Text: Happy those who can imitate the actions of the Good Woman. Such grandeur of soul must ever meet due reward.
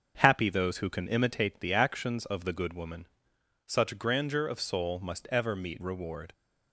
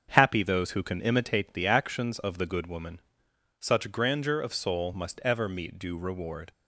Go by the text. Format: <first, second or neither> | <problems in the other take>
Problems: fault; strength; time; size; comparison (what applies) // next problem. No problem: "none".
second | starts louder than the rest; strong; until 1.2 s; 7 dB; strong in the second // skips "due"; at 5.8 s